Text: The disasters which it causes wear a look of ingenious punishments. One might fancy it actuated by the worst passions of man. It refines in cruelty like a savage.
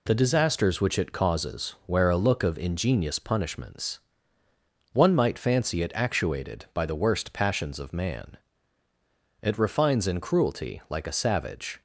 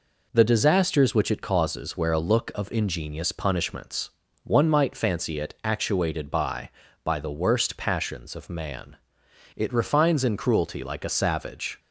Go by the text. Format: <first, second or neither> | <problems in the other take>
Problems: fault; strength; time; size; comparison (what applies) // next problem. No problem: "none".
first | says "by" twice; at 7.0 s